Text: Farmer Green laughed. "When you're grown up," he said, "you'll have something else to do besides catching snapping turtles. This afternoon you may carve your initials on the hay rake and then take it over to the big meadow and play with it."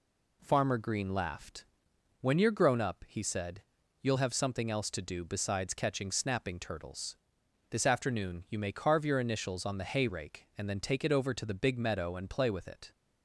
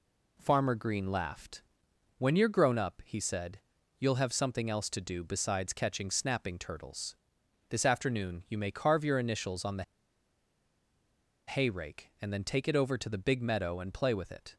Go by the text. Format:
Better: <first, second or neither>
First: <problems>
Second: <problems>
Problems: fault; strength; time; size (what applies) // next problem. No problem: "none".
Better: first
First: none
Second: pauses between "the" and "hay"; strong; at 9.8 s; 1.6 s long